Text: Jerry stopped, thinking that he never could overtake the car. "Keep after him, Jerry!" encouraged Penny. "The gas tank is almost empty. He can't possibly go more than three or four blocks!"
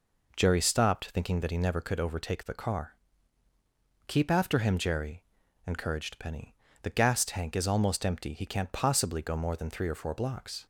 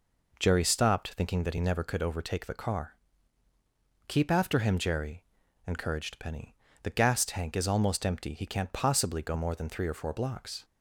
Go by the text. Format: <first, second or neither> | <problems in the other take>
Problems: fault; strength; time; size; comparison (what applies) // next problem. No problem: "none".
neither | none